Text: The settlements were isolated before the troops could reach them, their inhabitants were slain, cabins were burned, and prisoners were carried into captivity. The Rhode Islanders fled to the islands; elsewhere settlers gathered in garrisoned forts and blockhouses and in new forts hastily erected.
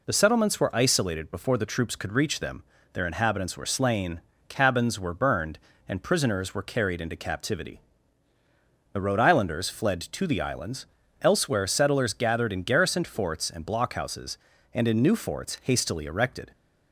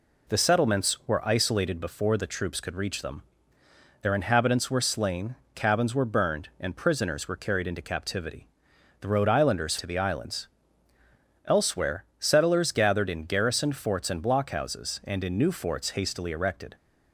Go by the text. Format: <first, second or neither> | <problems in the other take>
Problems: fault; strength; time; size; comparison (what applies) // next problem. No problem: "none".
first | skips "fled"; at 9.7 s // pauses between "elsewhere" and "settlers"; slight; at 12.0 s; 0.16 s long